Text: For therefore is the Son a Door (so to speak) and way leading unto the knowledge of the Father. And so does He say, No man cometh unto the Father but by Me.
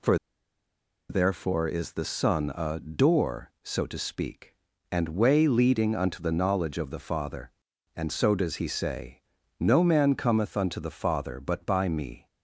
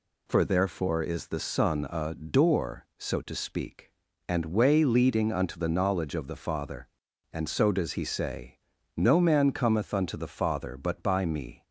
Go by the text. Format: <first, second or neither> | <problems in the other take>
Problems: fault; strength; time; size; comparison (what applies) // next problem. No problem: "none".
second | pauses between "For" and "therefore"; noticeable; at 0.1 s; 0.92 s long